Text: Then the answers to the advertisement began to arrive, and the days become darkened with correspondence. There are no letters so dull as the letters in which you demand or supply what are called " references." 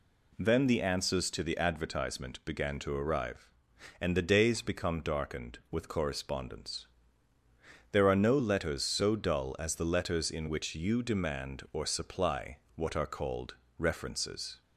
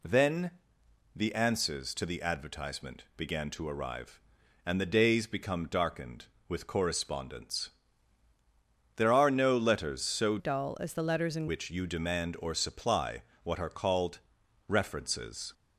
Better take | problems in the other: first | pauses between "Then" and "the"; noticeable; at 0.5 s; 0.64 s long // changes voice from "dull" to "in"; from 10.3 to 11.4 s; 1.1 s long // pauses between "supply" and "what"; slight; at 13.2 s; 0.20 s long; slight in the first

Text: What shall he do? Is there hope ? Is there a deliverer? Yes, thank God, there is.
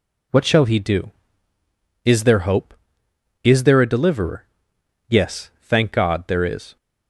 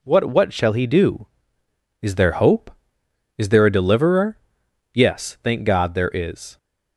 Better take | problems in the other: first | says "What" twice; at 0.2 s

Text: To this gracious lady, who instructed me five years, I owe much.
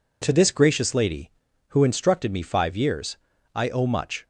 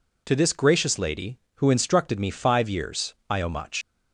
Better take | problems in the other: first | leaves "much" unfinished; at 3.8 s; 85 ms

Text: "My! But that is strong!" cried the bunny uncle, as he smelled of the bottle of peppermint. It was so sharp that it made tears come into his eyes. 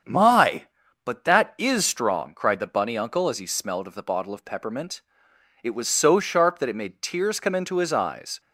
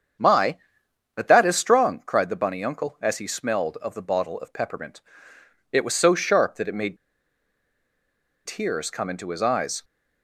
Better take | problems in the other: first | starts louder than the rest; strong; until 1.7 s; 7.5 dB; strong in the first // pauses between "made" and "tears"; strong; at 6.9 s; 1.5 s long

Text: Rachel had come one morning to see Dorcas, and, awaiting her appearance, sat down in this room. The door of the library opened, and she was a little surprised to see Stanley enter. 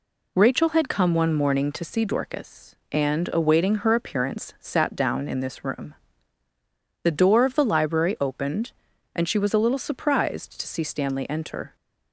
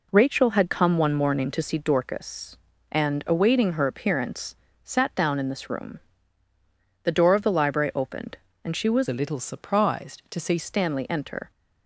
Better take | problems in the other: first | changes voice from "a" to "see"; from 9.0 to 10.5 s; 1.5 s long

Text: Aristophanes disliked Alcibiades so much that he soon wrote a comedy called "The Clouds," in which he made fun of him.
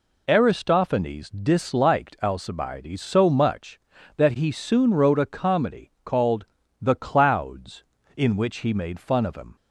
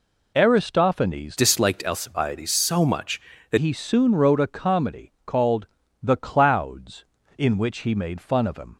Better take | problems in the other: first | changes voice from "disliked" to "that"; from 1.3 to 3.5 s; 2.2 s long // pauses between "called" and "The"; slight; at 5.6 s; 0.36 s long; slight in the first

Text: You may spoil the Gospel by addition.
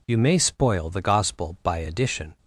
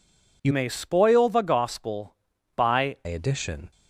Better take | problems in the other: first | changes voice from "may" to "by"; from 0.5 to 2.9 s; 2.4 s long

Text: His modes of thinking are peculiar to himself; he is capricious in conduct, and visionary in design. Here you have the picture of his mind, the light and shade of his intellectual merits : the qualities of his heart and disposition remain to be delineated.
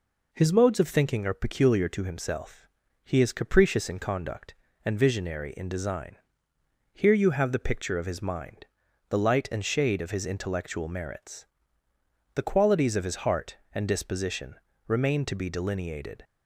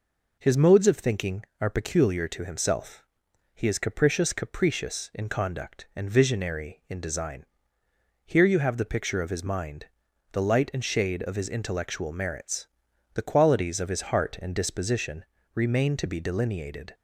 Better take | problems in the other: first | says "capricious" twice; at 4.3 s // pauses between "disposition" and "remain"; slight; at 15.2 s; 0.32 s long; slight in the first

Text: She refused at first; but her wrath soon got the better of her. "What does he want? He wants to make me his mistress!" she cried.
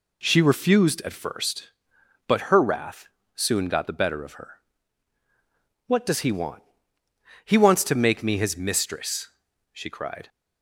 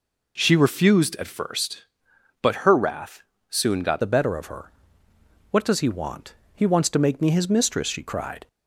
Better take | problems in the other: first | pauses between "wrath" and "soon"; slight; at 3.2 s; 0.26 s long; slight in the first // changes voice at "the"; from 4.0 s on; 4.4 s long

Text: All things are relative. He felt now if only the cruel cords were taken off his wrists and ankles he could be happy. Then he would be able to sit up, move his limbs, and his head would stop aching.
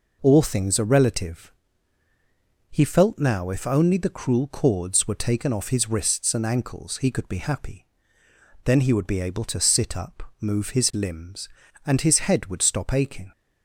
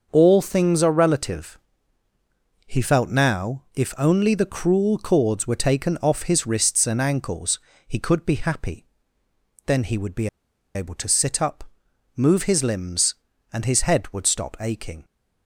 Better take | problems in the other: first | starts louder than the rest; until 1.1 s; 6.5 dB // pauses between "ankles" and "he"; slight; at 7.5 s; 0.28 s long // pauses between "be" and "able"; noticeable; at 10.2 s; 0.46 s long

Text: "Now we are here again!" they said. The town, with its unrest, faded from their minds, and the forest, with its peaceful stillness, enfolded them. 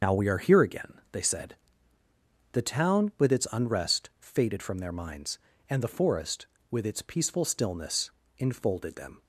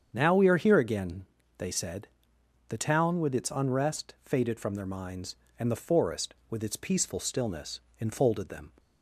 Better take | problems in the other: second | loses the start of "Now"; at 0.0 s; 65 ms // starts louder than the rest; until 1.1 s; 6.5 dB; strong in the second

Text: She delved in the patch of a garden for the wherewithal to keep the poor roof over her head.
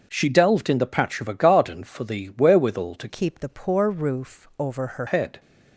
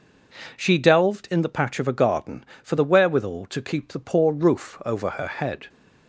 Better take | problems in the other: second | starts louder than the rest; until 1.1 s; 6.5 dB // changes voice from "keep" to "her"; from 3.0 to 5.0 s; 2.0 s long

